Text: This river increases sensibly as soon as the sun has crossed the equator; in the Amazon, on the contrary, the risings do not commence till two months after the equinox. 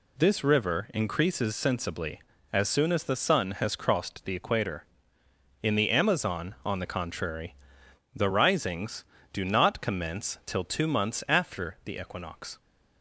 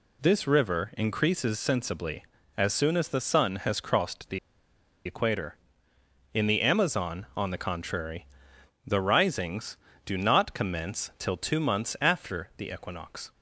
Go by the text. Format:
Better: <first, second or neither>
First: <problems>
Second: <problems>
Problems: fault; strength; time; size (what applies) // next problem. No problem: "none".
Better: first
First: none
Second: pauses between "the" and "equator"; noticeable; at 4.3 s; 0.67 s long